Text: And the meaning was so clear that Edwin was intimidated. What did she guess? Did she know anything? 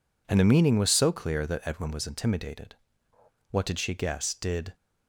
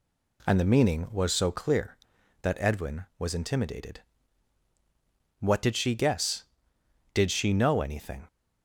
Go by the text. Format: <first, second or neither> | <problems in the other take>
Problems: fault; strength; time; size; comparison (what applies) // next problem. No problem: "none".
second | stops before "she know anything"; at 4.7 s